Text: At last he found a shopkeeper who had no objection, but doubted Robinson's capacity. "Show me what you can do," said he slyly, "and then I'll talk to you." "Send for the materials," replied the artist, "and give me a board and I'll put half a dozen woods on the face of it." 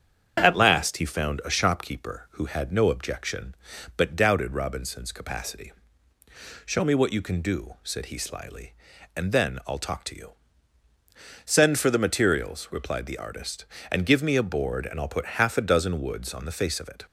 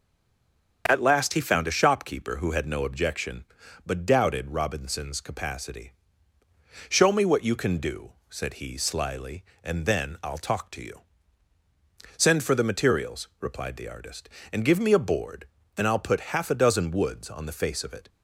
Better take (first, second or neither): first